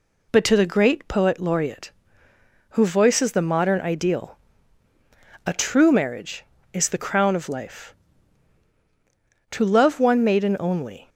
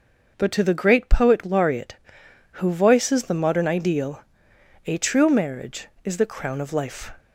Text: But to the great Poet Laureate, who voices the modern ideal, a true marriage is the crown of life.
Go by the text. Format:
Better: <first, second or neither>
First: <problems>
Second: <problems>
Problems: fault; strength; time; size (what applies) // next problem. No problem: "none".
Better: second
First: goes on to say "To love one maiden only"; from 9.5 s on; 1.5 s long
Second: none